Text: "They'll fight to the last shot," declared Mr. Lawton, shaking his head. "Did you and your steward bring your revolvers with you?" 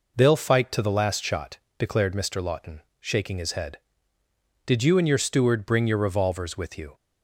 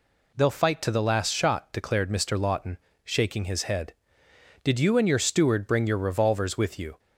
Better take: neither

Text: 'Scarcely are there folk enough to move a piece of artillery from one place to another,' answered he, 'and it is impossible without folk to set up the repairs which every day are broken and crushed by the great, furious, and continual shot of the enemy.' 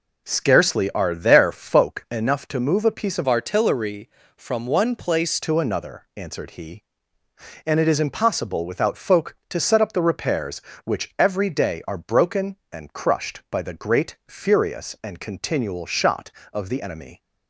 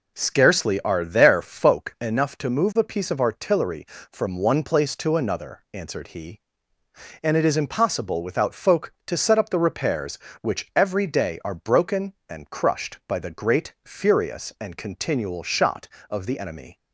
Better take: second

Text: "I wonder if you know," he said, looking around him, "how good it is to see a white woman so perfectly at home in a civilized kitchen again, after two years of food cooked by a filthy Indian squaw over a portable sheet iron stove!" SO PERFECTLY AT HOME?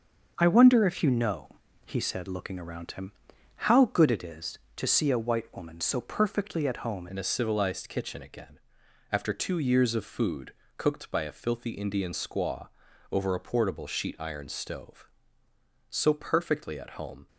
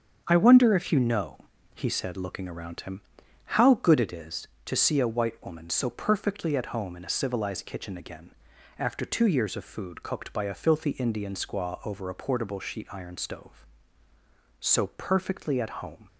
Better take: second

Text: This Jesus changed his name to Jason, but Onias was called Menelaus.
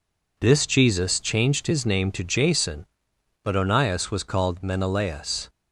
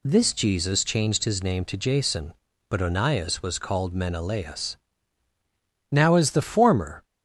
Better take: first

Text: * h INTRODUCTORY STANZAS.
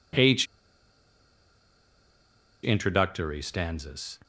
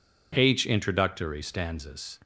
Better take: second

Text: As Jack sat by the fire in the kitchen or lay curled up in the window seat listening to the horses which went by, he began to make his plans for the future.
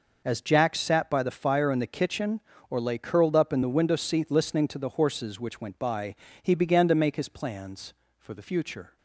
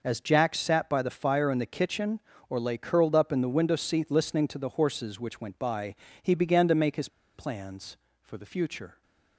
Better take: first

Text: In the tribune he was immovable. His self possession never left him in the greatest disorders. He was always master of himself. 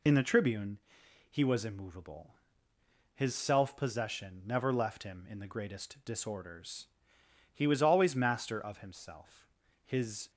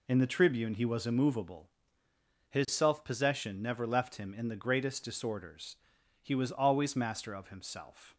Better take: second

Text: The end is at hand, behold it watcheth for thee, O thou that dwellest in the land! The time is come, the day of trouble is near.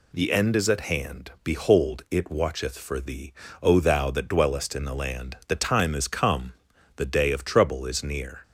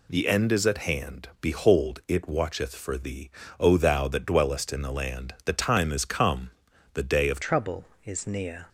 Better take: first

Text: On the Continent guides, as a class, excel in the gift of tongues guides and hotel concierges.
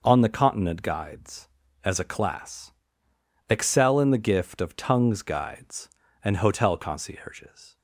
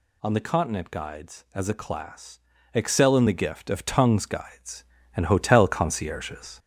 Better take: first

